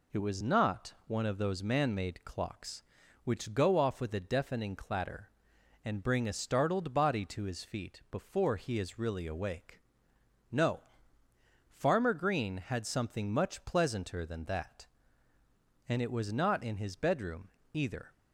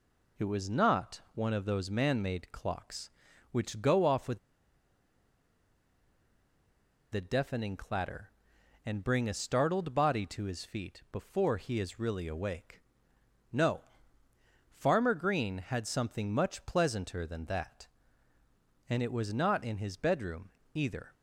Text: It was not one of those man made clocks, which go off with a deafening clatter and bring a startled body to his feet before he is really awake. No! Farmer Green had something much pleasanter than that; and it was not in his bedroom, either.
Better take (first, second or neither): first